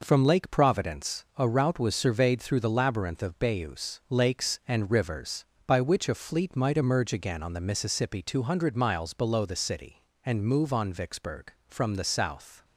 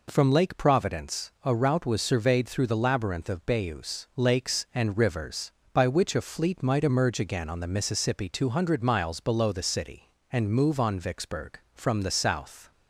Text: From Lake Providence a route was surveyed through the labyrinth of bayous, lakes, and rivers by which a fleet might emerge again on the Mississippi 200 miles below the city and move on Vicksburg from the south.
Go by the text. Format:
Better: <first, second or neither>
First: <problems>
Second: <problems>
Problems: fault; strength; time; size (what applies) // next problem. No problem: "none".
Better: second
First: gets quieter; throughout; 6.5 dB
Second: none